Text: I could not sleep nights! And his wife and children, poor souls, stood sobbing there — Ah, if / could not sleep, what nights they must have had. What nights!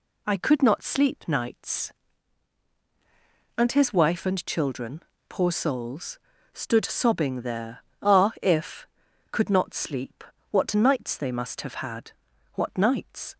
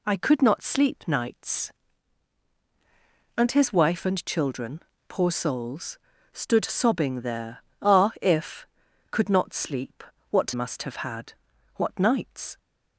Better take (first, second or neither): first